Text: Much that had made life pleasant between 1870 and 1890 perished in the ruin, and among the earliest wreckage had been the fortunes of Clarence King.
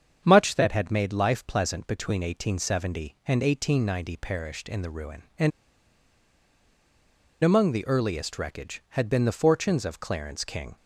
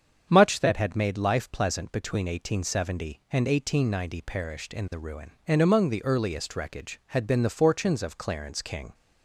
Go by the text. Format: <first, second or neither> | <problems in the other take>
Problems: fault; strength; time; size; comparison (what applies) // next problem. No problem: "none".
second | starts louder than the rest; strong; until 1.2 s; 7.5 dB; strong in the second // pauses between "and" and "among"; strong; at 5.5 s; 1.9 s long